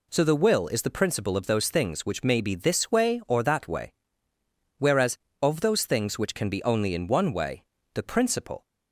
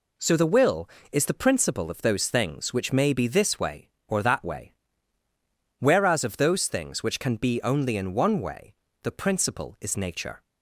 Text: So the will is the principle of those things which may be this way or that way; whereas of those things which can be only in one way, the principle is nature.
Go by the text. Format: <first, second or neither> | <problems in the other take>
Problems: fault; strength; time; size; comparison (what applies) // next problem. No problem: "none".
second | stops before "is nature"; at 8.6 s